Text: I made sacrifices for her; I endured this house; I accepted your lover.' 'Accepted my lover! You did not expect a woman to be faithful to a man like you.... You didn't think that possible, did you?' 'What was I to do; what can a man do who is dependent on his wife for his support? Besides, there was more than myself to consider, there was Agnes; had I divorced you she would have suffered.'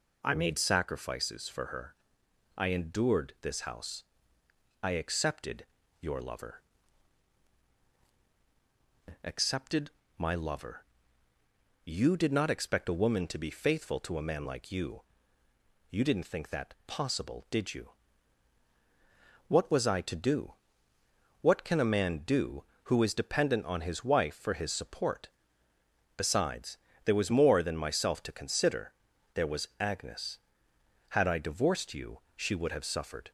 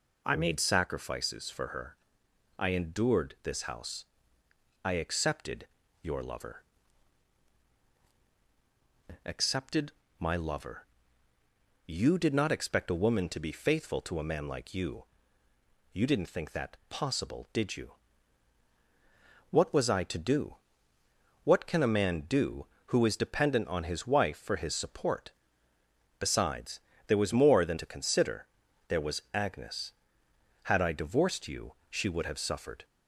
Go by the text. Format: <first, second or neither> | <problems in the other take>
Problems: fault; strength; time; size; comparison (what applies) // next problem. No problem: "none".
first | pauses between "accepted" and "your"; slight; at 5.6 s; 0.34 s long; slight in the first // pauses between "Accepted" and "my"; slight; at 9.9 s; 0.28 s long; slight in the first // skips "myself"; at 27.7 s // pauses between "you" and "she"; slight; at 31.7 s; 0.16 s long; slight in the first